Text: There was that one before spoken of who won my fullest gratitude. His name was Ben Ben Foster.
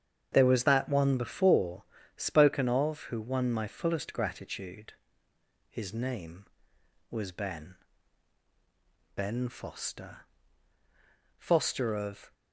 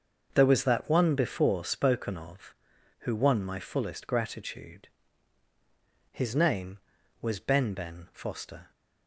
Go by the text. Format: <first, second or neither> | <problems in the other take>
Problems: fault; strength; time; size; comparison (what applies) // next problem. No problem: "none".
second | starts louder than the rest; strong; until 1.3 s; 8 dB; also in the second // pauses between "before" and "spoken"; slight; at 1.8 s; 0.34 s long // pauses between "Ben" and "Ben"; strong; at 7.7 s; 1.3 s long // goes on to say "Foster of"; noticeable; from 11.3 s on; 0.96 s long